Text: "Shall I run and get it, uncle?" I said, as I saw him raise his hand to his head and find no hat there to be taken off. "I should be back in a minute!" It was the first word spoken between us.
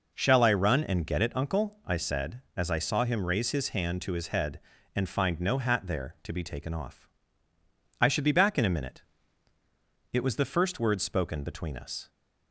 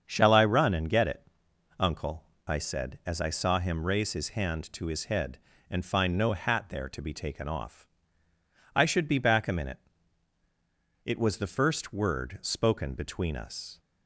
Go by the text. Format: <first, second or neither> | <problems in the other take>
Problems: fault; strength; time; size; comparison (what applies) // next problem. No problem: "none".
first | starts louder than the rest; strong; until 1.0 s; 7 dB // skips "in"; at 9.4 s